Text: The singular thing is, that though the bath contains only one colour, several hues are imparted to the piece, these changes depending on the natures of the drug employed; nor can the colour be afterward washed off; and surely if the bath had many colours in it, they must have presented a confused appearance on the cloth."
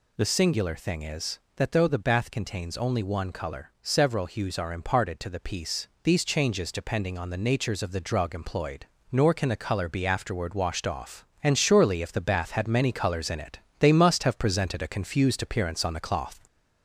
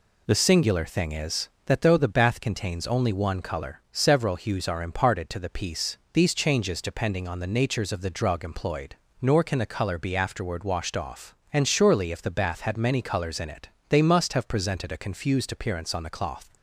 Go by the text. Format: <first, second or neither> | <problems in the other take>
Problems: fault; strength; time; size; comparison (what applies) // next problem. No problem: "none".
second | gets louder; slight; throughout; 2.5 dB